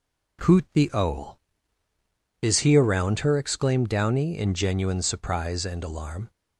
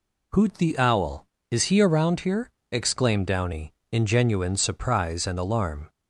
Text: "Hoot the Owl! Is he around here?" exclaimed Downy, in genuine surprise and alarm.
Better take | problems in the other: second | says "her" for "here"; at 3.2 s

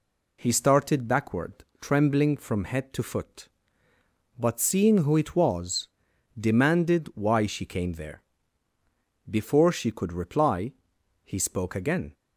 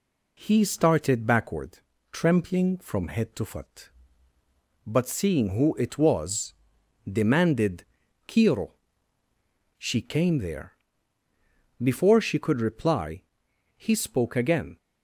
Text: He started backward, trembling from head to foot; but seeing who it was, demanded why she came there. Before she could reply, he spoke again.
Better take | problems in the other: first | says "kiro" for "why"; at 8.2 s

